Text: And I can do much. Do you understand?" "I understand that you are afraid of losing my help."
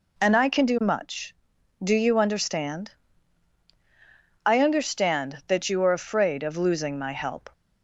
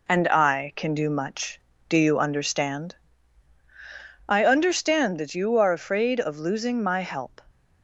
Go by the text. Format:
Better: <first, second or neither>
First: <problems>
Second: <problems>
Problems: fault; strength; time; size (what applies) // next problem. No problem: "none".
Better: neither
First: none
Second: none